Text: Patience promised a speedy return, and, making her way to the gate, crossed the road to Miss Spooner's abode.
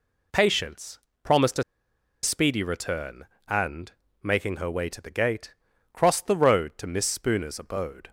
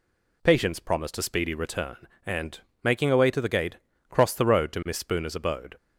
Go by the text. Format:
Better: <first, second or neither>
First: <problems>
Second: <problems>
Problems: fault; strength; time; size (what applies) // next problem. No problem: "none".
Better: second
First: pauses between "Patience" and "promised"; slight; at 0.9 s; 0.24 s long // pauses between "a" and "speedy"; noticeable; at 1.6 s; 0.60 s long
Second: none